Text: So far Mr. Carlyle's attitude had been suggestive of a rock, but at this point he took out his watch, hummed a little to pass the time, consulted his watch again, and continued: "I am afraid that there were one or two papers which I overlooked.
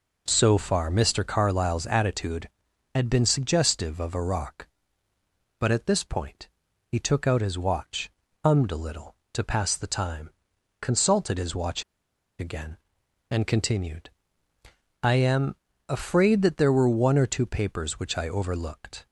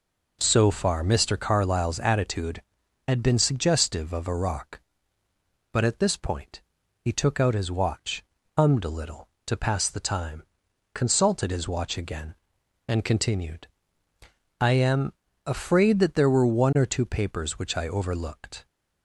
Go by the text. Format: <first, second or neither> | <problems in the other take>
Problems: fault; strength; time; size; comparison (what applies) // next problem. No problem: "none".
second | pauses between "point" and "he"; at 6.4 s; 0.42 s long; also in the second // pauses between "watch" and "again"; noticeable; at 11.8 s; 0.56 s long // pauses between "am" and "afraid"; slight; at 15.5 s; 0.34 s long; slight in the second